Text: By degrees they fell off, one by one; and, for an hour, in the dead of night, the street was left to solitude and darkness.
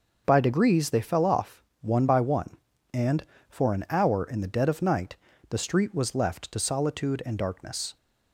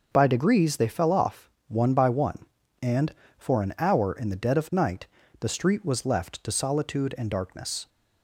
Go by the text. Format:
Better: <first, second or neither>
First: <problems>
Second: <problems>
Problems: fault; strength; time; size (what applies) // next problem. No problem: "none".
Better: neither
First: starts louder than the rest; noticeable; until 1.2 s; 6 dB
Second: starts louder than the rest; noticeable; until 1.1 s; 6 dB